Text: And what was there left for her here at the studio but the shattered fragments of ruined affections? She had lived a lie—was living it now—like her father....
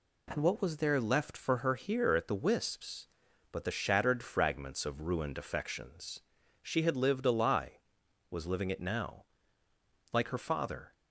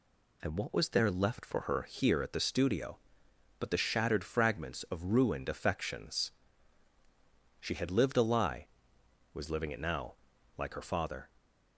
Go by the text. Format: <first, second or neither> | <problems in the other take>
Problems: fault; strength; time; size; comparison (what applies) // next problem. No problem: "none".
second | says "wisps" for "studio"; at 2.3 s